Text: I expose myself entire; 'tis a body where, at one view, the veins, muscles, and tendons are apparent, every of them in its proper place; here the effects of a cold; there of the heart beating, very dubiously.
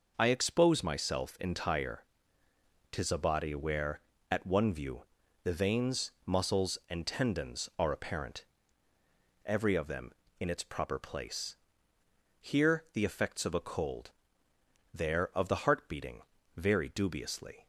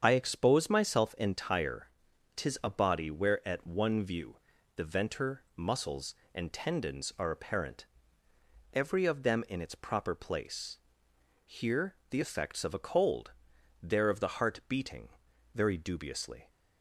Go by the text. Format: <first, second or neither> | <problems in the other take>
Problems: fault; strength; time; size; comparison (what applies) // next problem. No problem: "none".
first | starts louder than the rest; strong; until 1.0 s; 7.5 dB // says "venter" for "veins"; at 4.8 s